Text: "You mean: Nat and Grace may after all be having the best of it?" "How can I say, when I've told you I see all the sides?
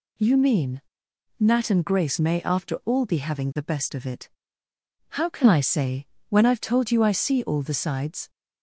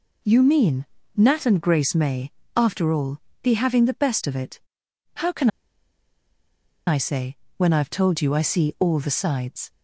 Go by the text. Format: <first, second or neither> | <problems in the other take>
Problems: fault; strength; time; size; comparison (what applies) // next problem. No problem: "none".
first | pauses between "may" and "after"; slight; at 2.2 s; 0.24 s long // pauses between "all" and "be"; slight; at 3.1 s; 0.22 s long // pauses between "can" and "I"; strong; at 5.4 s; 1.3 s long